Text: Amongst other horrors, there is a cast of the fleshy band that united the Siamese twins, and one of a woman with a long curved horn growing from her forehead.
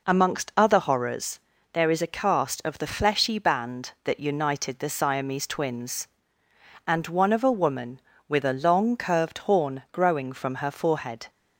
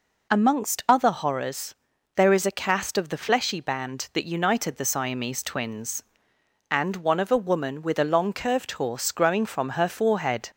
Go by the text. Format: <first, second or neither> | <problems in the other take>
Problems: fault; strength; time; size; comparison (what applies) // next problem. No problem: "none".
first | says "horse" for "horn"; at 8.7 s